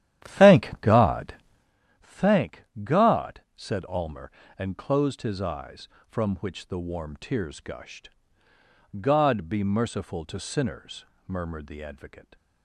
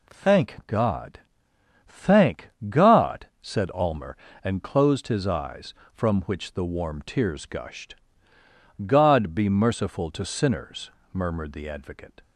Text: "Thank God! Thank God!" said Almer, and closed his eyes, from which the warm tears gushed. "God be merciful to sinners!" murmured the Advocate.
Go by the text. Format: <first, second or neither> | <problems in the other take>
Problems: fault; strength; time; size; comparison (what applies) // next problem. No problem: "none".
second | starts louder than the rest; strong; until 1.8 s; 11.5 dB // pauses between "Thank" and "God"; slight; at 2.6 s; 0.18 s long; slight in the second